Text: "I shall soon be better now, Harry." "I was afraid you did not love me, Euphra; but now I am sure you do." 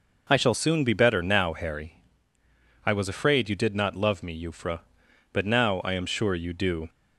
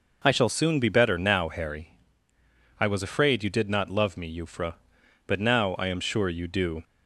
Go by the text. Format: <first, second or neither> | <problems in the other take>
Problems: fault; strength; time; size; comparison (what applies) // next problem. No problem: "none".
neither | none